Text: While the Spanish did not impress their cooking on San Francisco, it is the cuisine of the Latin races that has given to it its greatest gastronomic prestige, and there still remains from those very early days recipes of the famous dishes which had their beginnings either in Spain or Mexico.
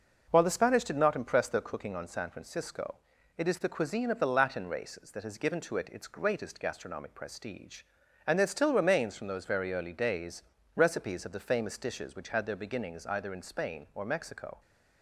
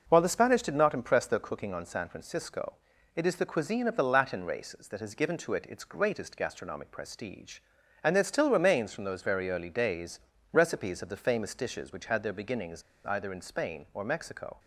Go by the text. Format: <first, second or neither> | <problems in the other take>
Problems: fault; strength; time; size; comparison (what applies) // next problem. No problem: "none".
first | pauses between "days" and "recipes"; slight; at 10.2 s; 0.32 s long; slight in the first // pauses between "beginnings" and "either"; slight; at 12.8 s; 0.25 s long